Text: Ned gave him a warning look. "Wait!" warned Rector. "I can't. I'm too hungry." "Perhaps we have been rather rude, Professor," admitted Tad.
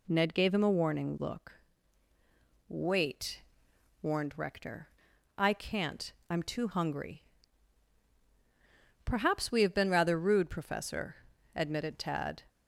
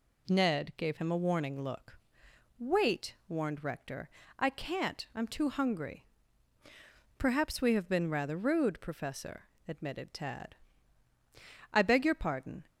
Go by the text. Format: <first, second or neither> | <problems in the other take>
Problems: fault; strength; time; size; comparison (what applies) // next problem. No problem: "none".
first | goes on to say "I beg your pardon"; noticeable; from 11.7 s on; 0.92 s long